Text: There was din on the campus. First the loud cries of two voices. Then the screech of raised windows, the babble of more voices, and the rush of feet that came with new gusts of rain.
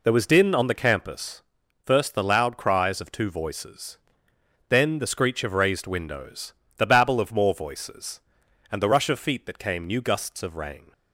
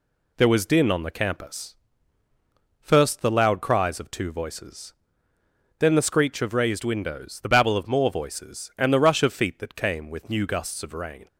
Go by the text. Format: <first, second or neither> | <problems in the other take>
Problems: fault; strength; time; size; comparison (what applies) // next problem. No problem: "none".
second | skips "with"; at 9.8 s